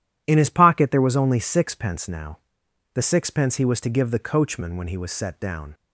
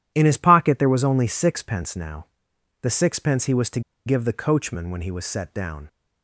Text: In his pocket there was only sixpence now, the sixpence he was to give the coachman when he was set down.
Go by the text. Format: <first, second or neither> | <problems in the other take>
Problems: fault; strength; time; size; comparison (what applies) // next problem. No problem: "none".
first | pauses between "to" and "give"; slight; at 3.8 s; 0.25 s long